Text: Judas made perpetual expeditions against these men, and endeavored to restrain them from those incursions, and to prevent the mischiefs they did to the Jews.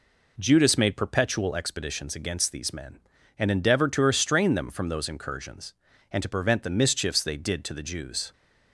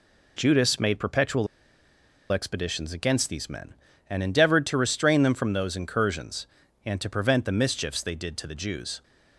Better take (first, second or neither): first